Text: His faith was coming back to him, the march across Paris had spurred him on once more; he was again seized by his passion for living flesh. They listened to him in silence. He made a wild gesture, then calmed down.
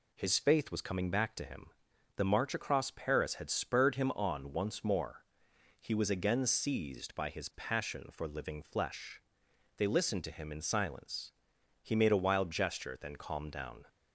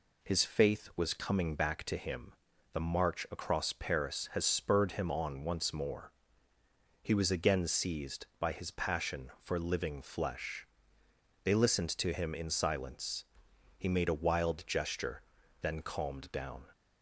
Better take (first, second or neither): first